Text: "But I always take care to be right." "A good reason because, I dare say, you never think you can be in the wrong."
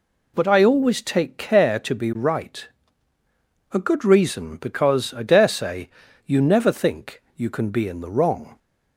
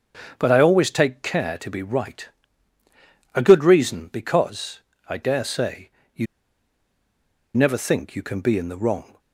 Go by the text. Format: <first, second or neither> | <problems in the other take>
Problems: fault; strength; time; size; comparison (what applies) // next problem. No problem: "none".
first | starts louder than the rest; strong; until 1.3 s; 7.5 dB // pauses between "you" and "never"; strong; at 6.2 s; 1.2 s long